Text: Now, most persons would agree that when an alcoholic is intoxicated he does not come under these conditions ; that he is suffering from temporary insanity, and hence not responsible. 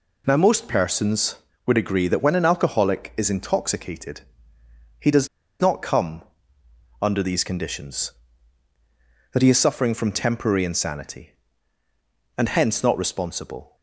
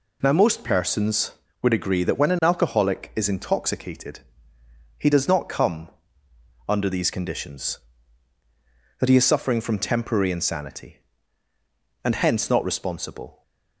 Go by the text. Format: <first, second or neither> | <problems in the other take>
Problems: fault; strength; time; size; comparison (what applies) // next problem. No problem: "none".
second | pauses between "intoxicated" and "he"; noticeable; at 4.2 s; 0.78 s long; noticeable in the second // pauses between "does" and "not"; slight; at 5.2 s; 0.33 s long // pauses between "come" and "under"; noticeable; at 6.2 s; 0.76 s long; noticeable in the second